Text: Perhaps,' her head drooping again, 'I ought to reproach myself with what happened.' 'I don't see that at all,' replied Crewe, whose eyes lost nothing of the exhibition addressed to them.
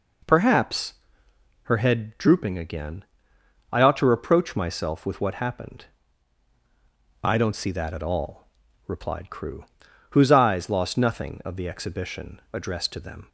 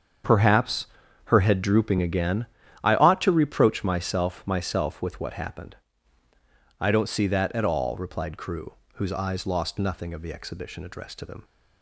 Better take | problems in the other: first | starts louder than the rest; strong; until 1.6 s; 7 dB // says "myself" twice; at 4.4 s

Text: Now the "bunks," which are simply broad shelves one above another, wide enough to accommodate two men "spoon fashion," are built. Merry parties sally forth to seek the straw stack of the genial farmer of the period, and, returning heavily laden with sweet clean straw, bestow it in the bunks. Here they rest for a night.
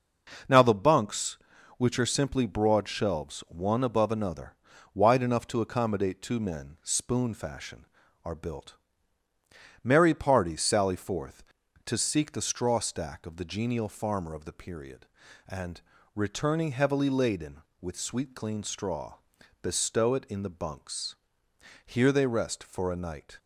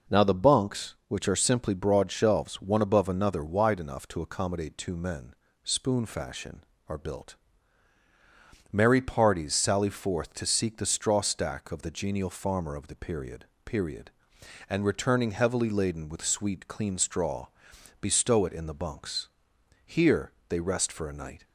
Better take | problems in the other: first | pauses between "men" and "spoon"; slight; at 5.3 s; 0.30 s long // says "period" twice; at 13.6 s // pauses between "Here" and "they"; slight; at 20.3 s; 0.16 s long

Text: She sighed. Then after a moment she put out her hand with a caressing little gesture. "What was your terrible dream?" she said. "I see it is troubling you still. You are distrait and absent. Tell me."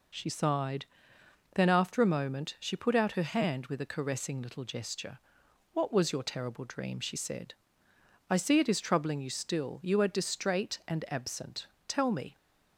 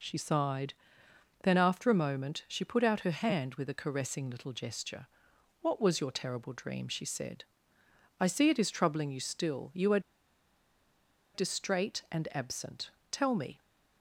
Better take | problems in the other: first | pauses between "are" and "distrait"; strong; at 9.9 s; 1.3 s long

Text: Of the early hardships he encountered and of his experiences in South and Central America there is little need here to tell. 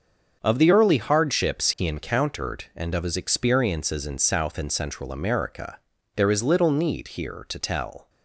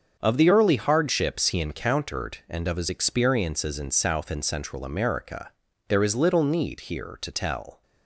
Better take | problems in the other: neither | starts louder than the rest; the same in both // pauses between "America" and "there"; the same in both

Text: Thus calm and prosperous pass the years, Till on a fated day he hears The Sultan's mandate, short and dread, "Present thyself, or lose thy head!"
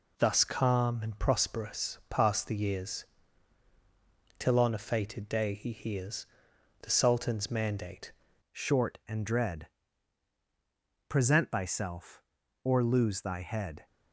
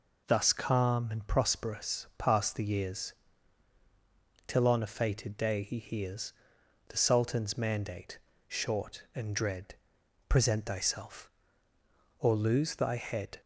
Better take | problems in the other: second | pauses between "hears" and "The"; noticeable; at 6.2 s; 0.56 s long; noticeable in the second // changes voice at "short"; from 8.5 s on; 5.3 s long

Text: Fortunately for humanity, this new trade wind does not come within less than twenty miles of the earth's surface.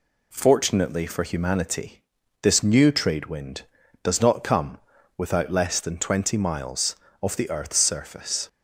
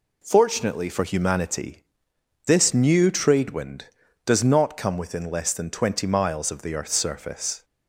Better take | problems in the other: second | says "without" for "within"; at 5.1 s

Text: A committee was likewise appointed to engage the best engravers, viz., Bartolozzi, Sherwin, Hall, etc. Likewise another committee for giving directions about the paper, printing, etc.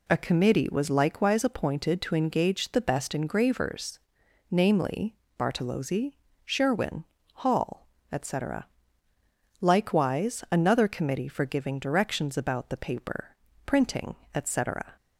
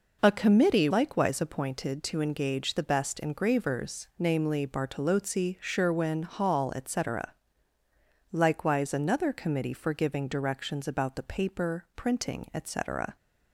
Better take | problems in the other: first | skips "was"; at 0.9 s

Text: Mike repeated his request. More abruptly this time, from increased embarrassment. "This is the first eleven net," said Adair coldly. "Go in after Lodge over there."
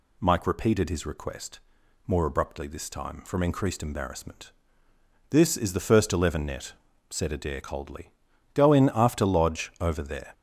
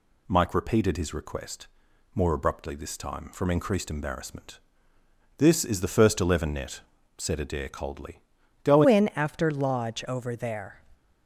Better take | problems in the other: first | changes voice at "in"; from 8.8 s on; 2.0 s long

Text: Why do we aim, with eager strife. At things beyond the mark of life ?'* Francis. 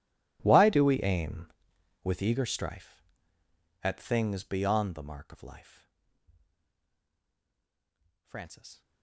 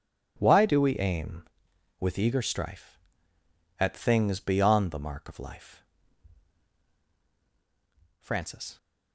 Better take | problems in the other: second | gets quieter; strong; throughout; 49 dB // starts louder than the rest; strong; until 1.4 s; 19 dB; strong in the second

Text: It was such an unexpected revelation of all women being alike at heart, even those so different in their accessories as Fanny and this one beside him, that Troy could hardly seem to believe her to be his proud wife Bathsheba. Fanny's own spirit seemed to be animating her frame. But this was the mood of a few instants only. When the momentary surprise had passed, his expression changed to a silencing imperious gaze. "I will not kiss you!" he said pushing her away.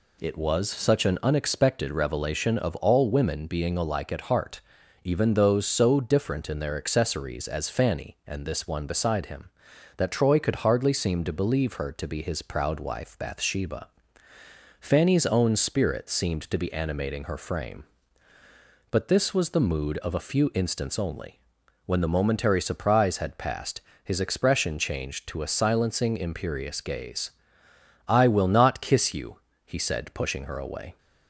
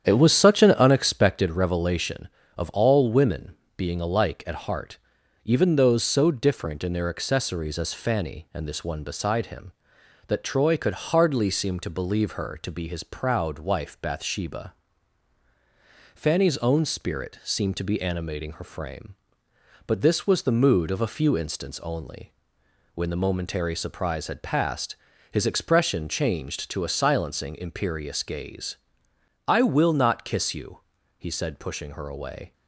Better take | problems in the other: first | starts louder than the rest; strong; until 1.6 s; 9 dB // pauses between "women" and "being"; slight; at 3.5 s; 0.20 s long

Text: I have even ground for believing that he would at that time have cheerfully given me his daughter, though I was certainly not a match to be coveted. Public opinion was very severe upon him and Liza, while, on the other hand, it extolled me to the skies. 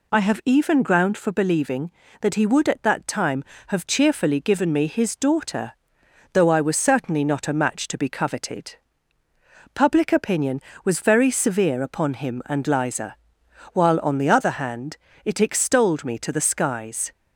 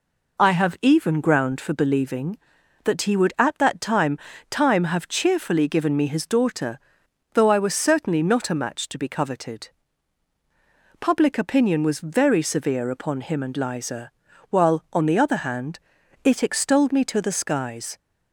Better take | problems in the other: first | says "time" twice; at 4.5 s

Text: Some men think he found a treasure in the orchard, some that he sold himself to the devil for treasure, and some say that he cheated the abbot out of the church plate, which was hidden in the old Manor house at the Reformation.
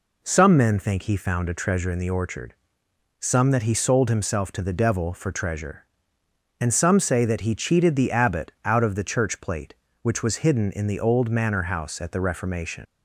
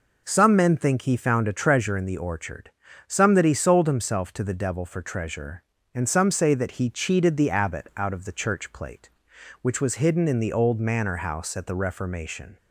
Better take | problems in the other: second | leaves "Reformation" unfinished; at 12.8 s; 80 ms

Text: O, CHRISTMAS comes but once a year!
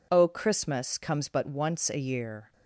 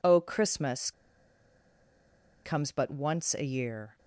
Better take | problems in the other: first | pauses between "CHRISTMAS" and "comes"; strong; at 0.9 s; 1.5 s long

